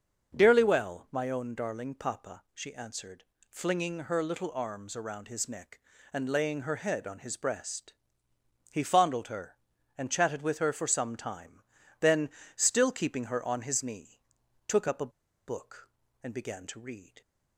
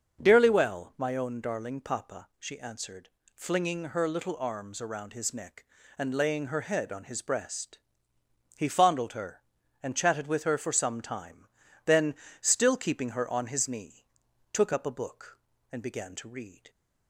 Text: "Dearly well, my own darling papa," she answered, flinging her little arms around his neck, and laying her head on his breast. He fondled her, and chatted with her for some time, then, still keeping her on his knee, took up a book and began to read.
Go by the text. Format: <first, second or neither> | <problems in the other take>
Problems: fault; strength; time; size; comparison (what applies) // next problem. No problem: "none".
second | starts louder than the rest; until 1.4 s; 6 dB; also in the second // pauses between "a" and "book"; at 15.1 s; 0.36 s long